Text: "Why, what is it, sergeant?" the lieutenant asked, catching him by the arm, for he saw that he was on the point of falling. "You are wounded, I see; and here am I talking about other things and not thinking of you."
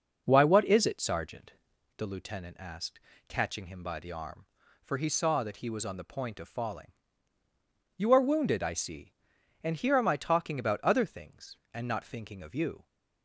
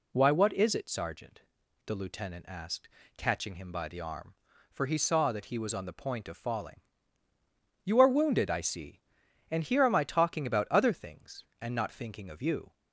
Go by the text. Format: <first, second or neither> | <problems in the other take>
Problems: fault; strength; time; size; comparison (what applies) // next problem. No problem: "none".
second | starts louder than the rest; noticeable; until 2.0 s; 5.5 dB